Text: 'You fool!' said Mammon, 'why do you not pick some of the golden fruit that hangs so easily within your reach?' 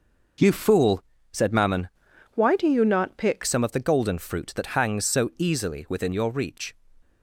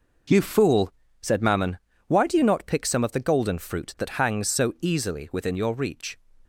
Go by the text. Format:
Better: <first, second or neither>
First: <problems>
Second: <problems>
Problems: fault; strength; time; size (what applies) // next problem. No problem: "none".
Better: second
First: changes voice from "why" to "pick"; from 2.3 to 3.4 s; 1.1 s long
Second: none